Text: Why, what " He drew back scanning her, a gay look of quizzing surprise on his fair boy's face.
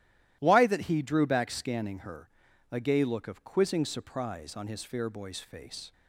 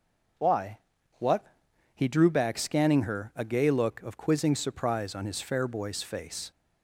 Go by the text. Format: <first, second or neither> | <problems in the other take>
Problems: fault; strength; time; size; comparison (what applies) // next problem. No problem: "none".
second | starts louder than the rest; strong; until 1.4 s; 14 dB // says "that" for "what"; at 0.6 s